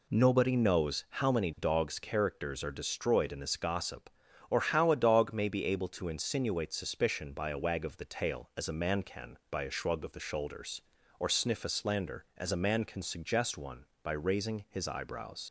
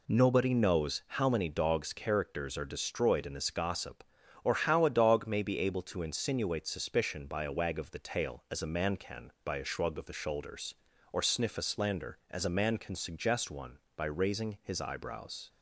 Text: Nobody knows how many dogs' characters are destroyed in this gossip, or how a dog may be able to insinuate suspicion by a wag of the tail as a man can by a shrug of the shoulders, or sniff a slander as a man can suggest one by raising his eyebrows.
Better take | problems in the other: second | leaves "eyebrows" unfinished; at 15.4 s; 70 ms

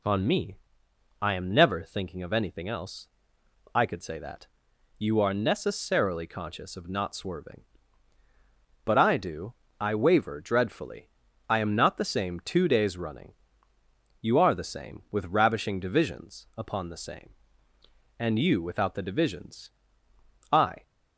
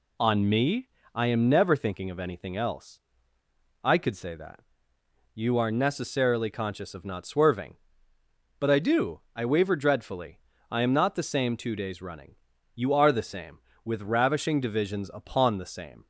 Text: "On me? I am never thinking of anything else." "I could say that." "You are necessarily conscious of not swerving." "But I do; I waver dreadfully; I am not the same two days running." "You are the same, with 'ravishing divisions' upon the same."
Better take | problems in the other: second | goes on to say "And you without the divisions I"; strong; from 18.1 s on; 2.6 s long

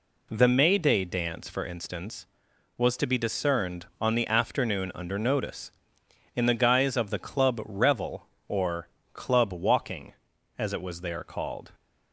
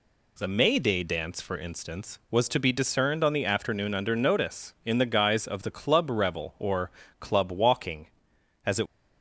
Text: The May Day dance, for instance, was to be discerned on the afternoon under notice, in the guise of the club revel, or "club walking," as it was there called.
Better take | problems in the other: first | pauses between "or" and "club"; slight; at 6.9 s; 0.28 s long; slight in the first // stops before "was there called"; at 8.8 s

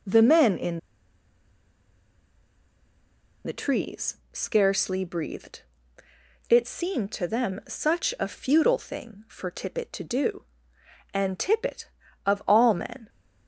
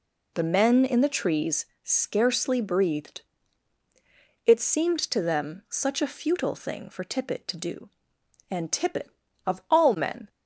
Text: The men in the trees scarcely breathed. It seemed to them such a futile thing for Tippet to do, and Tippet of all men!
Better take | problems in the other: second | pauses between "in" and "the"; strong; at 0.7 s; 2.6 s long // pauses between "trees" and "scarcely"; slight; at 4.1 s; 0.16 s long; slight in the second

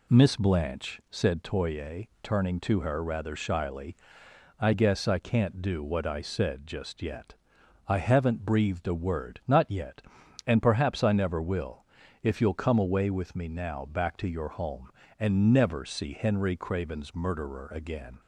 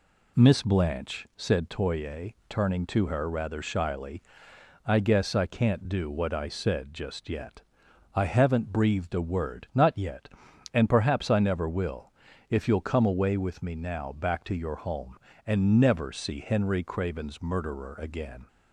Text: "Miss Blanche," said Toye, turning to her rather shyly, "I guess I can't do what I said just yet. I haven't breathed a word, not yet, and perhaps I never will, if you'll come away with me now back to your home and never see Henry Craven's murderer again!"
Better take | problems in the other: neither | none

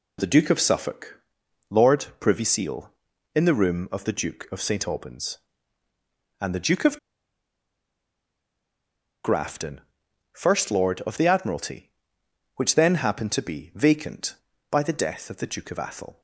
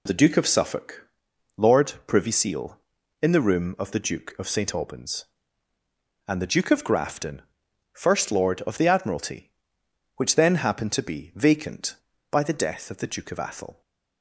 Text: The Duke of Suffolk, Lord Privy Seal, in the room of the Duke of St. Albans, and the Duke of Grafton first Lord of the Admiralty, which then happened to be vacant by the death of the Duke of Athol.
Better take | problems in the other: second | pauses between "of" and "Grafton"; strong; at 6.9 s; 2.2 s long // pauses between "Grafton" and "first"; noticeable; at 9.8 s; 0.50 s long; noticeable in the second

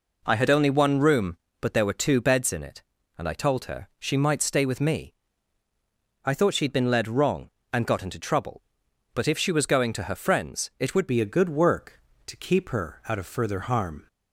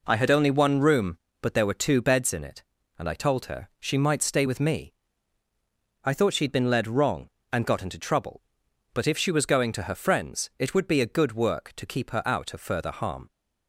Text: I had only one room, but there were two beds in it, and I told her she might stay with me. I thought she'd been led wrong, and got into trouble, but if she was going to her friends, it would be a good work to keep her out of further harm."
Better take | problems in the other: second | changes voice at "be"; from 11.0 s on; 3.0 s long

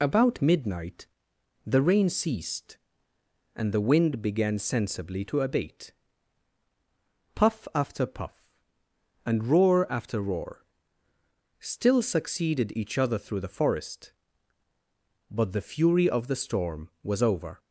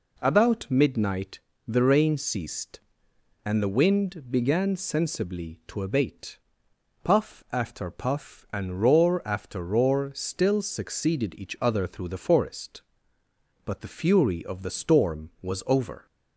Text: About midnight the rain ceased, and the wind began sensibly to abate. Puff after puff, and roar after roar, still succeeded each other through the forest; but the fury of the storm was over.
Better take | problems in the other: second | loses the start of "About"; at 0.0 s; 30 ms // pauses between "midnight" and "the"; noticeable; at 1.0 s; 0.60 s long; slight in the second

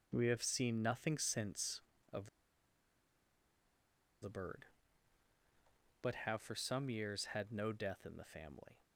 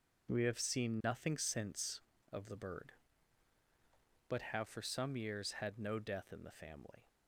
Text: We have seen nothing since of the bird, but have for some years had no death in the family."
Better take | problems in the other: second | pauses between "of" and "the"; strong; at 2.2 s; 1.9 s long

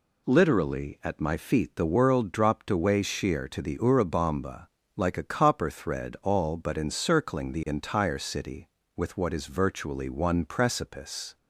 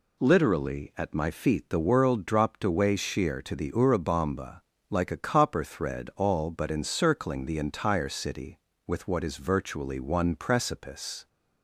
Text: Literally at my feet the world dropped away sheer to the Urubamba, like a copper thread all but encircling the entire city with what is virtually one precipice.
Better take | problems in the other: neither | none

